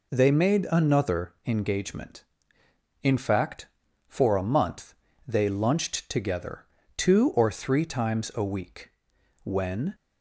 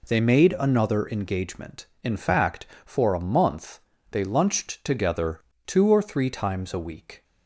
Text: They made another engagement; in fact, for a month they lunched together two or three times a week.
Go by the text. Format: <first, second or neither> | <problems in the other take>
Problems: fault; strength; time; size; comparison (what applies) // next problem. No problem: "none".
second | pauses between "month" and "they"; slight; at 4.9 s; 0.32 s long; slight in the second // pauses between "together" and "two"; slight; at 6.6 s; 0.32 s long; slight in the second // goes on to say "When"; from 9.4 s on; 0.50 s long